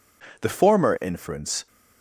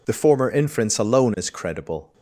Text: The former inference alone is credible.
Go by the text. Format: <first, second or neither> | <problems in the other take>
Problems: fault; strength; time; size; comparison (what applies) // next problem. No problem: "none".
second | stops before "alone is credible"; at 1.6 s